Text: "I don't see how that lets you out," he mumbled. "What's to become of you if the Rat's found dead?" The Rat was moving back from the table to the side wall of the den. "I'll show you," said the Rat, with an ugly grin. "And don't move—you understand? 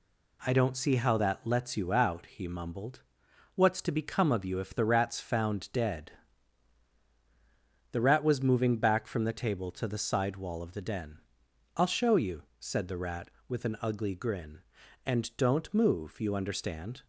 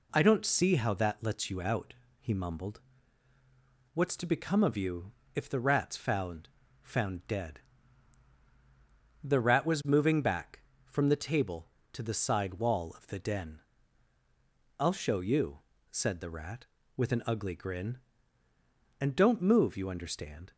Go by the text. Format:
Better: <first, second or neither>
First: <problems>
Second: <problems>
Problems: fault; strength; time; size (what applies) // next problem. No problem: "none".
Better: first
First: none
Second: pauses between "you" and "if"; slight; at 5.1 s; 0.22 s long // says "found" twice; at 6.8 s